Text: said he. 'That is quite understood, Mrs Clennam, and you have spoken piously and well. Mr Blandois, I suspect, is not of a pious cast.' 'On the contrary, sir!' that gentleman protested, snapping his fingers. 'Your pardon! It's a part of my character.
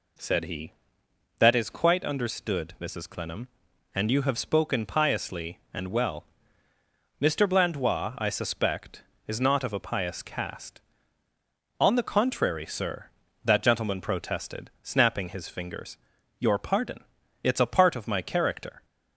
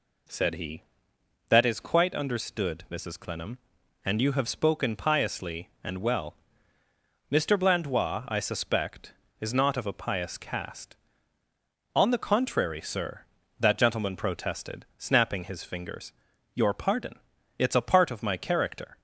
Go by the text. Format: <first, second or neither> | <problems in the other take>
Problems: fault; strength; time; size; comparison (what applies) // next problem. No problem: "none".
neither | none